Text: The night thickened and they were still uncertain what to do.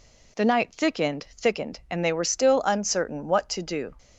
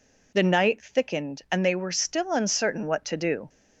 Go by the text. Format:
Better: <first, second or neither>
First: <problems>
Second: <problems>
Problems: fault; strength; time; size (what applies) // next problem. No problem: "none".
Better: second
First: says "thickened" twice; at 1.3 s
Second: none